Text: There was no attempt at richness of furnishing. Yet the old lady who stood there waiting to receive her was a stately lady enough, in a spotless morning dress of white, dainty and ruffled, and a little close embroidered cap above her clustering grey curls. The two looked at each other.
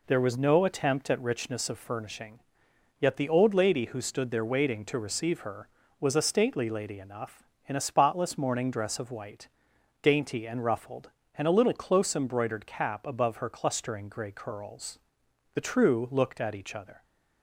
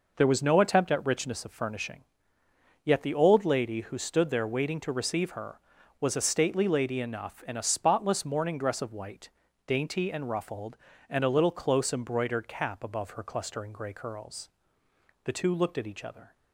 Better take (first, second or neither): second